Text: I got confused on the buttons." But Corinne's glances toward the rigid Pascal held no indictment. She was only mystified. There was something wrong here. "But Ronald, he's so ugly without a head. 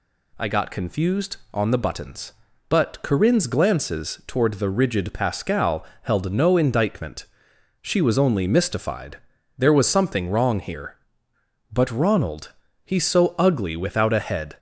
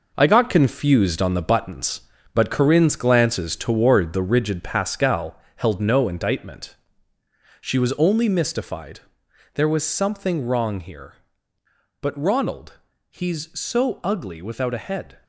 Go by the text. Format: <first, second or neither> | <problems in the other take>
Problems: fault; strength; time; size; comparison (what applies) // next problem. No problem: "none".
first | gets quieter; strong; throughout; 9 dB // pauses between "Pascal" and "held"; slight; at 5.3 s; 0.16 s long; slight in the first